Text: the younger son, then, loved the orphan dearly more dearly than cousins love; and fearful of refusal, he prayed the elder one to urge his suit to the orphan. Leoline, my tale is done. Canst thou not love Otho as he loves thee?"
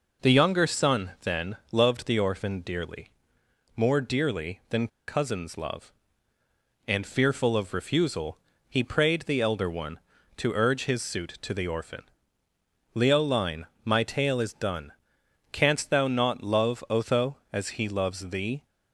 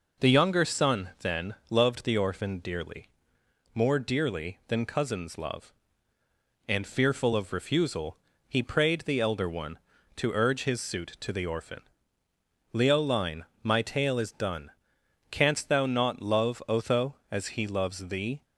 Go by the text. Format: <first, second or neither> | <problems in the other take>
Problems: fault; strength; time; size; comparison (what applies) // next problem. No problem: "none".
second | pauses between "dearly" and "more"; noticeable; at 3.0 s; 0.70 s long; noticeable in the second // pauses between "than" and "cousins"; slight; at 4.8 s; 0.20 s long